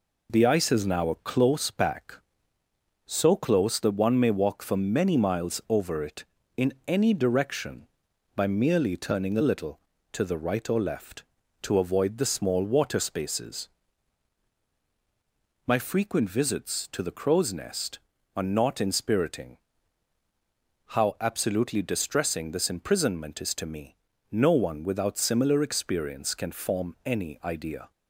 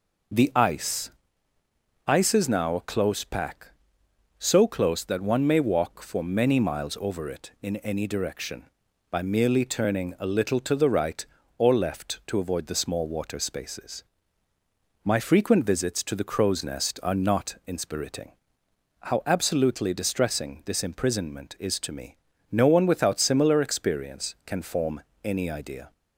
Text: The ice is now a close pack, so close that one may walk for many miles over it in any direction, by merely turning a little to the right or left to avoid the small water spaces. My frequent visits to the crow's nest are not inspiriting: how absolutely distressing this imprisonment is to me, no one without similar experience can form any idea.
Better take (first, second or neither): first